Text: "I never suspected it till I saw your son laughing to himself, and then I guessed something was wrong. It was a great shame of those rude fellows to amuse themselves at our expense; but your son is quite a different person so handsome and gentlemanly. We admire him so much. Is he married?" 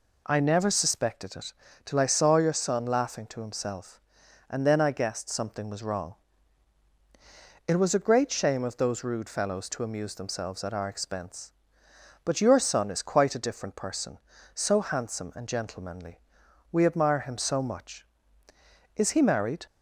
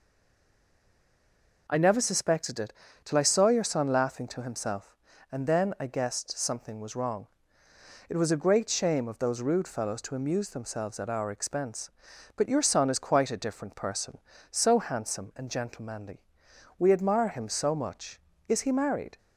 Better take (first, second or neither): first